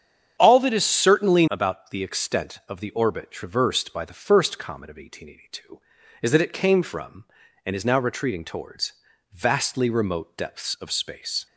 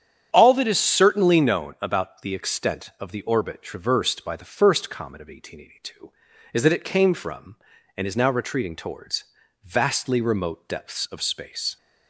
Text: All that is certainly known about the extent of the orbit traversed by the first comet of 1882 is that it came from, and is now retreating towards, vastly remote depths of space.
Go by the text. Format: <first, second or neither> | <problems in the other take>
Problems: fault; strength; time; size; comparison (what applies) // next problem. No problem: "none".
second | starts louder than the rest; strong; until 1.4 s; 8 dB; strong in the second // skips "known"; at 1.4 s